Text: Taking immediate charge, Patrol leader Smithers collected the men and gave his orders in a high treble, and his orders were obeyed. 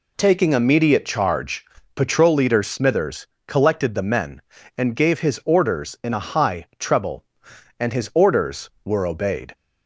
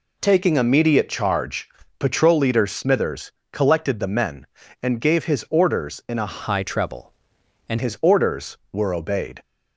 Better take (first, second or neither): first